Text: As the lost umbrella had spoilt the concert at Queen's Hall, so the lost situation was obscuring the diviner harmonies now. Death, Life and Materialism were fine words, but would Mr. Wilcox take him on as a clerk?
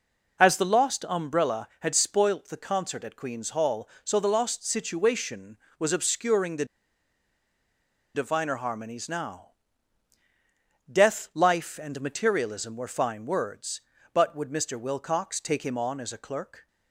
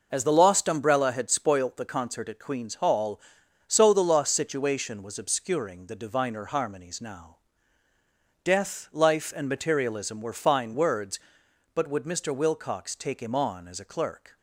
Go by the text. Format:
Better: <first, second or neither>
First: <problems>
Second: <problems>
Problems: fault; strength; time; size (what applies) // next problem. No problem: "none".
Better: second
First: pauses between "the" and "diviner"; strong; at 6.6 s; 1.4 s long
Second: none